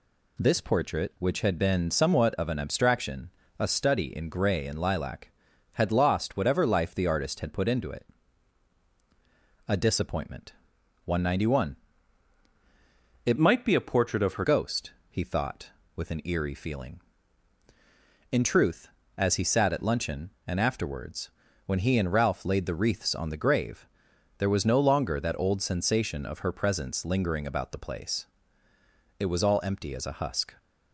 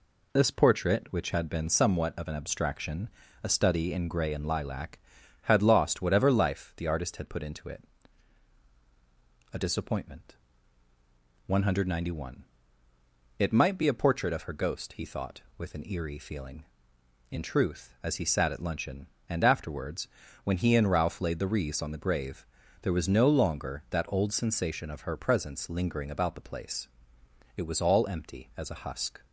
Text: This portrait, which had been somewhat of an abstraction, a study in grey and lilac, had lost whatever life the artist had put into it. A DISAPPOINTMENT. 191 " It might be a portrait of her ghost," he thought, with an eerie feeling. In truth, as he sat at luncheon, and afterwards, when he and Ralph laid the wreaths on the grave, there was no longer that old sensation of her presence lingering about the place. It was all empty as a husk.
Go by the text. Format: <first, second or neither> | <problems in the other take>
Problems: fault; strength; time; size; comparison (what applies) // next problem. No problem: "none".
second | changes voice from "might" to "her"; from 13.3 to 14.4 s; 1.1 s long